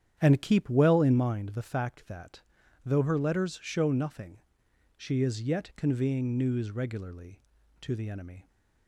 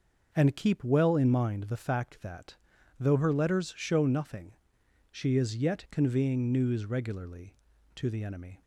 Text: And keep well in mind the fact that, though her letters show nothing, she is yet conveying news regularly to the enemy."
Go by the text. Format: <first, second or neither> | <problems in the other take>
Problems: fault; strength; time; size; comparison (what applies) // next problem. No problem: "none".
second | starts louder than the rest; strong; until 1.2 s; 9.5 dB